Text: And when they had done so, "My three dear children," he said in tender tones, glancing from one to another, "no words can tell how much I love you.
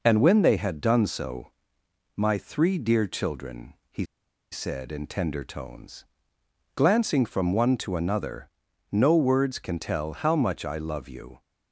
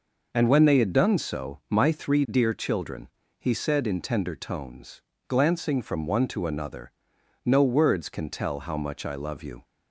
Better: second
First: pauses between "he" and "said"; noticeable; at 4.0 s; 0.46 s long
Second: none

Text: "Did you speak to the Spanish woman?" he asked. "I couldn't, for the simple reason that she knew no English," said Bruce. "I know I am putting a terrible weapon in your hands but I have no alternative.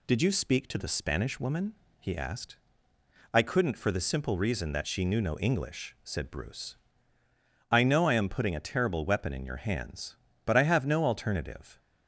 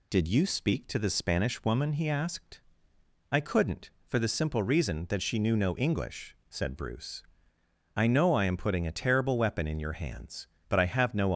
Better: first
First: none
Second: stops before "alternative"; at 11.3 s

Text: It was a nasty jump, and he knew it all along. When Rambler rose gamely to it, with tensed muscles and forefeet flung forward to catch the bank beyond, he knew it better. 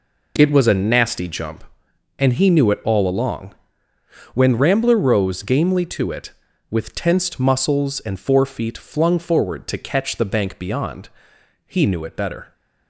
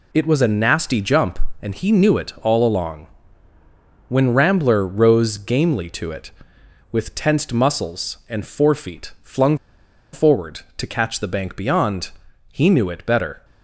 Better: first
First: none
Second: pauses between "flung" and "forward"; noticeable; at 9.5 s; 0.57 s long

